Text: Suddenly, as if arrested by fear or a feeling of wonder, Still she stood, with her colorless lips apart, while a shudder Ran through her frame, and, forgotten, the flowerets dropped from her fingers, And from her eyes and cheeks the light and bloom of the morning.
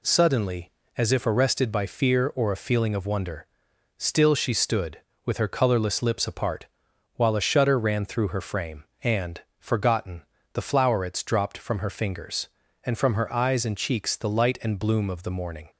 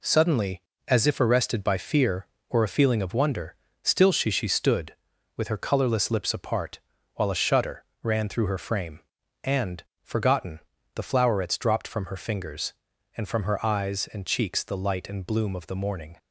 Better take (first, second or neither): first